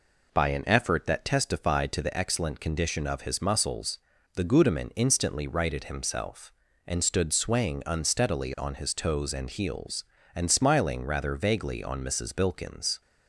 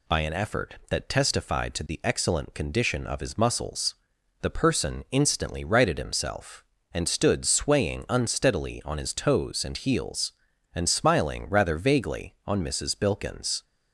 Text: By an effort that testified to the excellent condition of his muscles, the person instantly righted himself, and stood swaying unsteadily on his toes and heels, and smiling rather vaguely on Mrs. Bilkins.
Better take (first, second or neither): second